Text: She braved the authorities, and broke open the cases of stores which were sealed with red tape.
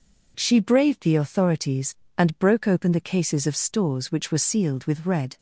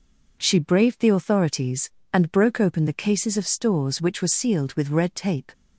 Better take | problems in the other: second | stops before "tape"; at 5.3 s

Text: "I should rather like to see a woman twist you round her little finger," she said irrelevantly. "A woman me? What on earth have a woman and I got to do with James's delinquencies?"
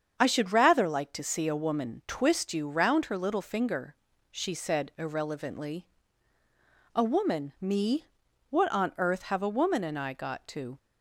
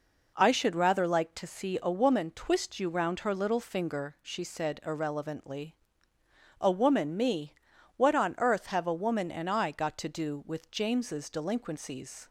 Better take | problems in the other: second | starts louder than the rest; strong; until 1.1 s; 7.5 dB // stops before "do with James's delinquencies"; at 10.7 s

